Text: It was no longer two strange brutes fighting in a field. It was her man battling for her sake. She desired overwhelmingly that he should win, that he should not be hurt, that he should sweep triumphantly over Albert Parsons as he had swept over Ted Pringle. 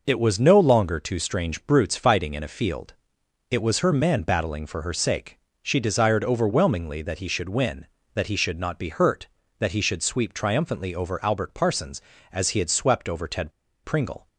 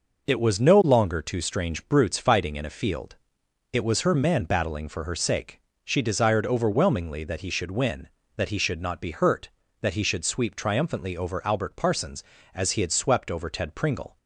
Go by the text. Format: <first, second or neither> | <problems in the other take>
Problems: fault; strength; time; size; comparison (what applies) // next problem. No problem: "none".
second | pauses between "Ted" and "Pringle"; slight; at 13.5 s; 0.32 s long